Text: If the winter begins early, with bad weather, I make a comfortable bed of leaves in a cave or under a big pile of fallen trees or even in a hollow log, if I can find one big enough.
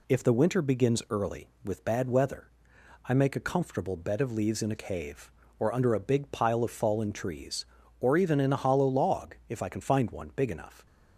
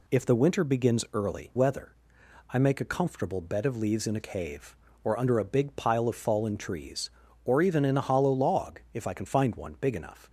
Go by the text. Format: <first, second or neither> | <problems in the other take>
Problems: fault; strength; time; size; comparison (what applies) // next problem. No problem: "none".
first | skips "with bad"; at 1.5 s